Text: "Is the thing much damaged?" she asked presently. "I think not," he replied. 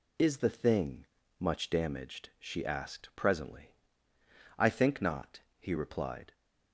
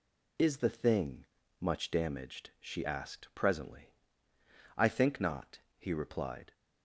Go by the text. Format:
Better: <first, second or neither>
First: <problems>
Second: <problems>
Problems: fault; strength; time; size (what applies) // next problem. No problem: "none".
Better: neither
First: pauses between "thing" and "much"; slight; at 1.0 s; 0.33 s long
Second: pauses between "thing" and "much"; slight; at 1.2 s; 0.34 s long